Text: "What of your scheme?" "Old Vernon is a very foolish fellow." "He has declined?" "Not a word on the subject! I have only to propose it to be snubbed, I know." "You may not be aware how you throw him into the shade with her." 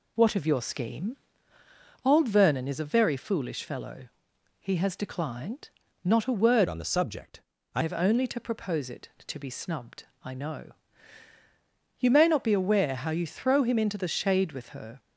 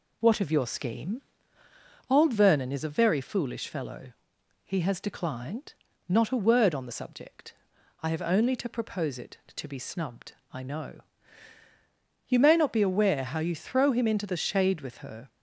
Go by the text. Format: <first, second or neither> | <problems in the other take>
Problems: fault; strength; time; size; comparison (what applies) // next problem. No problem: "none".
second | changes voice from "on" to "I"; from 6.6 to 7.8 s; 1.2 s long